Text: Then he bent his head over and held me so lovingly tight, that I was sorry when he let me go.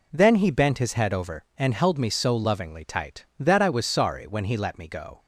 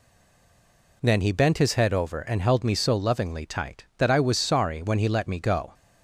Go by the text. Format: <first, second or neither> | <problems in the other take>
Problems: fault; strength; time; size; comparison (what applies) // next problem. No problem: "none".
first | stays silent before the first word; until 1.0 s; 1.0 s long